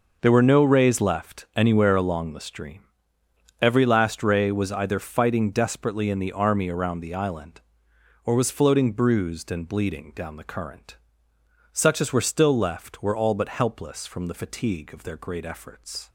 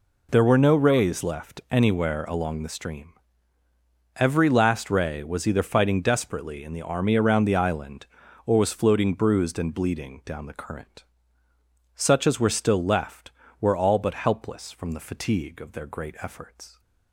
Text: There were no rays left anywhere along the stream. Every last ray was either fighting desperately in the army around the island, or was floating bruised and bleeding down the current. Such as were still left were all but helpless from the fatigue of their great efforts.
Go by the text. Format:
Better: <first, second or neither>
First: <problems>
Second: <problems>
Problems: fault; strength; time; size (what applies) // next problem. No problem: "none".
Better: neither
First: none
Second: none